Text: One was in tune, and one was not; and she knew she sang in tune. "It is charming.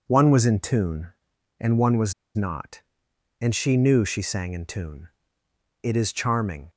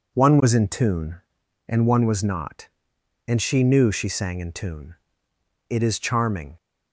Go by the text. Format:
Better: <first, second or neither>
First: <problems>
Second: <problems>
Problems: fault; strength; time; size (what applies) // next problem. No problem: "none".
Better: second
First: pauses between "was" and "not"; slight; at 2.1 s; 0.23 s long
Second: none